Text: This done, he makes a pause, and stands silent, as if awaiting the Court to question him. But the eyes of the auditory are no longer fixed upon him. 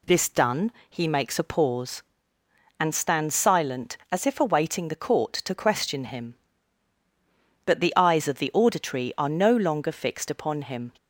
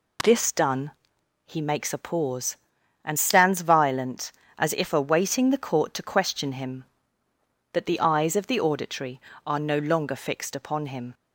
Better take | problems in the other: first | says "violent" for "silent"; at 3.6 s

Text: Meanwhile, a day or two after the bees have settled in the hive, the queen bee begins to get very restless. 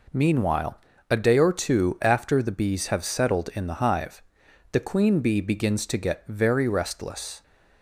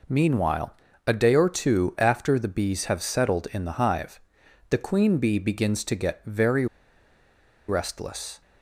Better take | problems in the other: first | pauses between "very" and "restless"; at 6.6 s; 1.0 s long

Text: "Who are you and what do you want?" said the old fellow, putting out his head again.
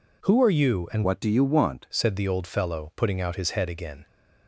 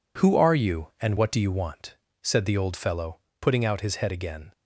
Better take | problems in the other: second | changes voice from "what" to "want"; from 1.0 to 1.8 s; 0.8 s long

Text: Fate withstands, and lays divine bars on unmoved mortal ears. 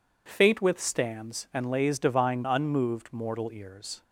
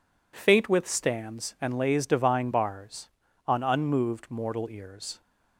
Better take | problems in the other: second | skips "bars on"; at 2.4 s

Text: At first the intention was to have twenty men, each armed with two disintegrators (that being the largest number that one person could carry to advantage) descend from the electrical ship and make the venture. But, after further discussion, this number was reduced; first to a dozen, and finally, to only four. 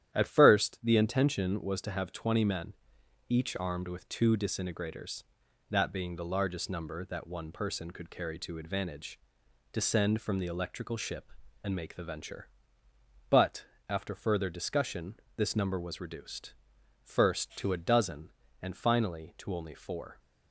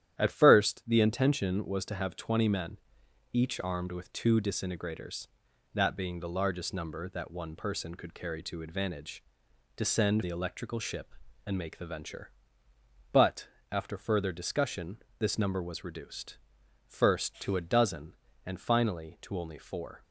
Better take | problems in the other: first | starts louder than the rest; strong; until 1.2 s; 11 dB; strong in the first // skips "from"; at 10.2 s

